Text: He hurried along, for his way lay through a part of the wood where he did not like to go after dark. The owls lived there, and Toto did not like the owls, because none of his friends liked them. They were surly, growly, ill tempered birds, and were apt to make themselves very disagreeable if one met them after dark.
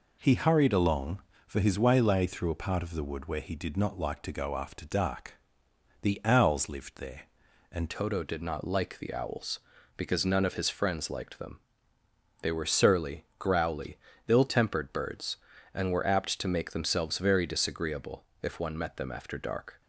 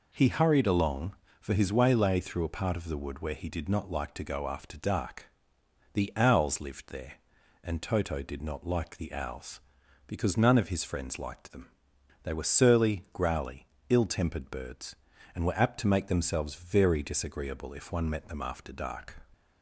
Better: second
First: changes voice at "Toto"; from 7.9 s on; 11.9 s long // pauses between "disagreeable" and "if"; slight; at 18.2 s; 0.18 s long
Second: none

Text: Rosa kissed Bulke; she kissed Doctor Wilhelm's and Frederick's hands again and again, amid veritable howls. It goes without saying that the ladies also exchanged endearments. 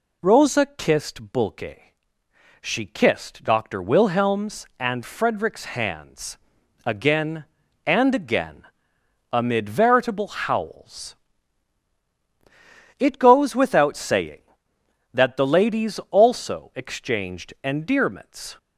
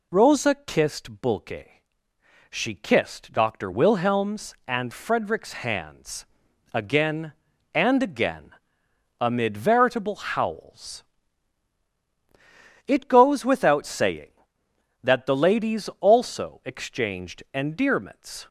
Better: neither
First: pauses between "hands" and "again"; noticeable; at 6.3 s; 0.48 s long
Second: pauses between "hands" and "again"; noticeable; at 6.2 s; 0.48 s long

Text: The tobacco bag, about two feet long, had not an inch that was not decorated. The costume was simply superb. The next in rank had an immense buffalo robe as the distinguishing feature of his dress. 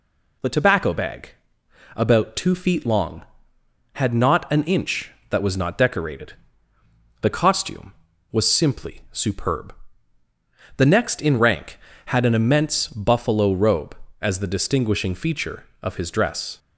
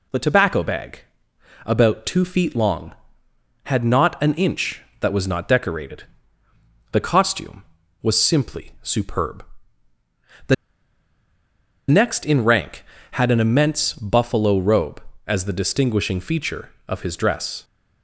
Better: first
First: none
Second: pauses between "The" and "next"; strong; at 10.5 s; 1.3 s long

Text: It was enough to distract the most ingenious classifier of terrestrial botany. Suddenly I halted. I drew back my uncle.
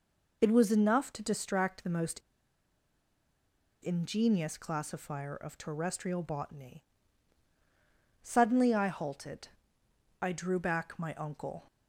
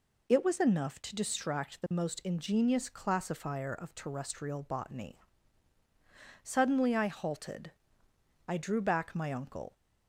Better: second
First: pauses between "most" and "ingenious"; strong; at 2.1 s; 1.6 s long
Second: none

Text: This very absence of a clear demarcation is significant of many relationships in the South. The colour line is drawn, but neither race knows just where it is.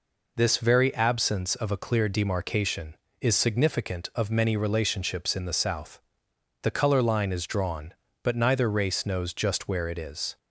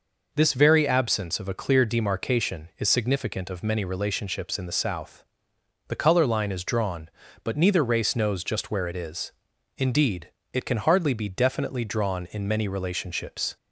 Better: first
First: none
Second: goes on to say "Indeed it can hardly be definitely drawn in many relationships"; strong; from 9.7 s on; 3.8 s long

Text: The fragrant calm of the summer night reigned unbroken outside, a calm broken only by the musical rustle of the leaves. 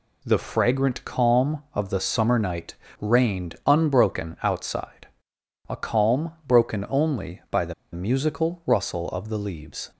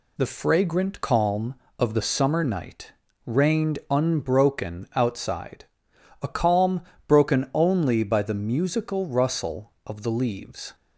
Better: second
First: pauses between "night" and "reigned"; slight; at 2.7 s; 0.26 s long // pauses between "calm" and "broken"; slight; at 6.3 s; 0.16 s long // pauses between "the" and "musical"; slight; at 7.7 s; 0.19 s long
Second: pauses between "night" and "reigned"; slight; at 2.9 s; 0.32 s long // pauses between "calm" and "broken"; slight; at 6.8 s; 0.26 s long

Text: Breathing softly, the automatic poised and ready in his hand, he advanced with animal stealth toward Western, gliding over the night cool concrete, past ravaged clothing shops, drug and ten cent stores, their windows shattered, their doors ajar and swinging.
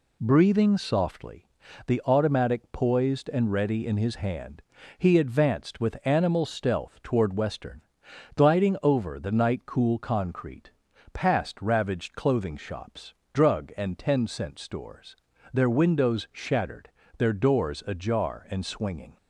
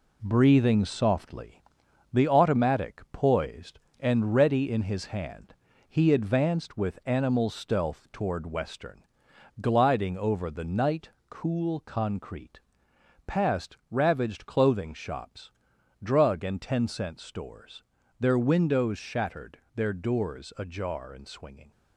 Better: first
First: none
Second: gets quieter; noticeable; throughout; 5.5 dB // pauses between "night" and "cool"; slight; at 11.0 s; 0.22 s long

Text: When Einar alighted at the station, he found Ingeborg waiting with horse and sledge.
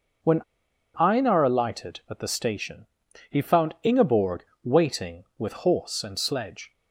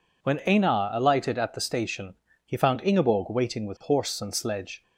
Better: second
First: pauses between "When" and "Einar"; noticeable; at 0.4 s; 0.54 s long // pauses between "Ingeborg" and "waiting"; slight; at 4.4 s; 0.18 s long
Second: none

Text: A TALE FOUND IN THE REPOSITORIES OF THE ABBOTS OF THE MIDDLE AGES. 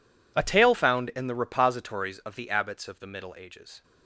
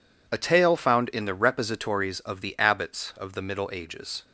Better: neither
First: none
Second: none

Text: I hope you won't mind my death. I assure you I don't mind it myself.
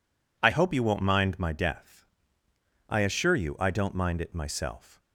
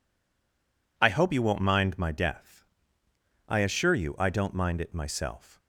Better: first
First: none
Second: stays silent before the first word; until 0.9 s; 0.9 s long

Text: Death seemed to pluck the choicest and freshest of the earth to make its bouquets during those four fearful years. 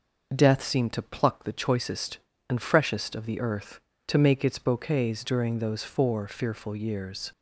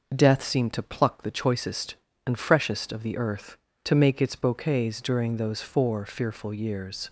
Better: neither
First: none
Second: none

